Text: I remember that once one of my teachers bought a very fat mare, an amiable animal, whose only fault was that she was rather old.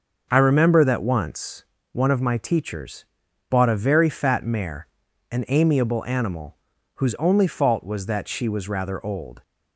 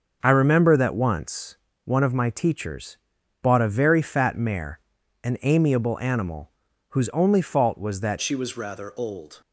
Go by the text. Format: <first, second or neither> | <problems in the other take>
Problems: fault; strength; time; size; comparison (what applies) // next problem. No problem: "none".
first | starts louder than the rest; until 1.2 s; 6 dB; noticeable in the first // pauses between "once" and "one"; slight; at 1.5 s; 0.30 s long; slight in the first // pauses between "teachers" and "bought"; at 2.9 s; 0.42 s long; also in the first // changes voice at "she"; from 8.2 s on; 1.2 s long